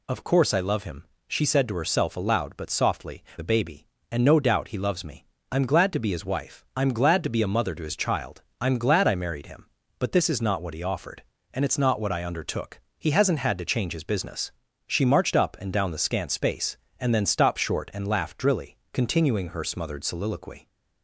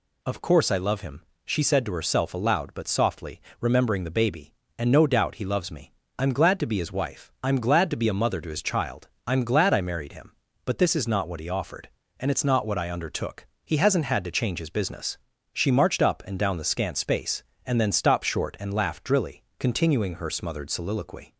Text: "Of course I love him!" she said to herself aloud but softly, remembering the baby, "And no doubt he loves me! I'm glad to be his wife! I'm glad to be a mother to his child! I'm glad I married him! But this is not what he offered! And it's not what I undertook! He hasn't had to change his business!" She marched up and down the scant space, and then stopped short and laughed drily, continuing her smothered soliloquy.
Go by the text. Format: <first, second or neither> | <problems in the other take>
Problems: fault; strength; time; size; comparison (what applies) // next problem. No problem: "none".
second | skips "remembering"; at 3.3 s